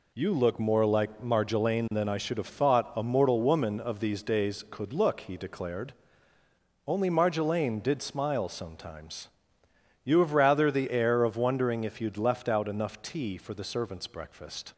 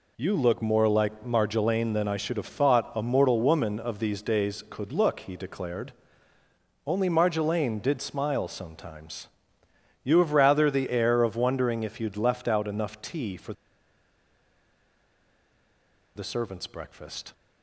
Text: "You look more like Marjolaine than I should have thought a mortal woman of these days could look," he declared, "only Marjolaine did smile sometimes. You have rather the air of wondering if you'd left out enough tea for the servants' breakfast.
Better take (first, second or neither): first